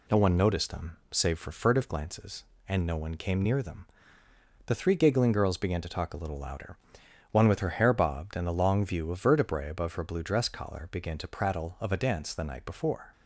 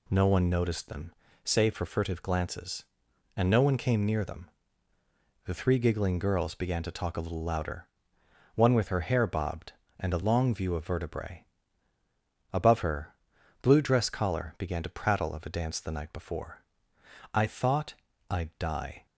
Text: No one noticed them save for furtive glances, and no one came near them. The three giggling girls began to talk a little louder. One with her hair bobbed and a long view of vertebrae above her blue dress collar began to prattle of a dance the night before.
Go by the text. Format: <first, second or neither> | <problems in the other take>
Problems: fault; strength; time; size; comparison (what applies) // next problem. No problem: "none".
first | pauses between "them" and "save"; slight; at 1.1 s; 0.32 s long // pauses between "vertebrae" and "above"; at 11.4 s; 1.0 s long // pauses between "her" and "blue"; noticeable; at 13.1 s; 0.48 s long // goes on to say "I thought I'd die"; strong; from 17.3 s on; 1.7 s long